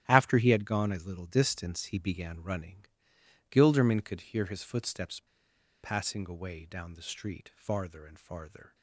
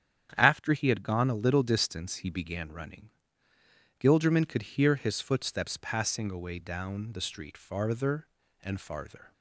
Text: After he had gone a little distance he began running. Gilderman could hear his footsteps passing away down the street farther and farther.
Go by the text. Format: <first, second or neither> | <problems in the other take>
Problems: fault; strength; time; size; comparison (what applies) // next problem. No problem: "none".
second | starts louder than the rest; strong; until 1.0 s; 11.5 dB; strong in the second // pauses between "footsteps" and "passing"; noticeable; at 5.2 s; 0.61 s long